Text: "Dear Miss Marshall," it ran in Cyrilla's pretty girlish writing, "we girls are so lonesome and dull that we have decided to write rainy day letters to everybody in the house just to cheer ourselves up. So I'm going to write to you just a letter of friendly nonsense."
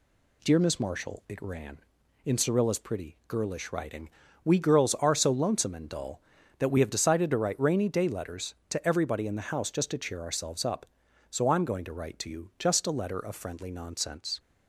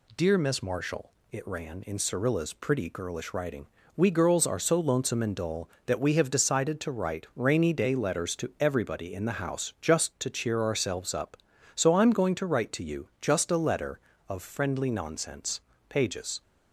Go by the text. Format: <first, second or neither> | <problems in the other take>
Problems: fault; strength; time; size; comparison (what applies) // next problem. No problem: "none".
first | goes on to say "Pages"; from 15.8 s on; 0.54 s long